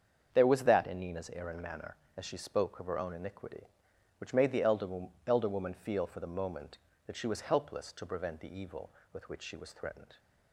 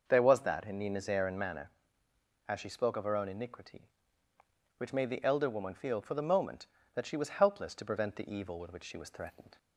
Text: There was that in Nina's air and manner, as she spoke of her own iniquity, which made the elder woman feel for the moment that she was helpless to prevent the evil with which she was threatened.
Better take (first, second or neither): second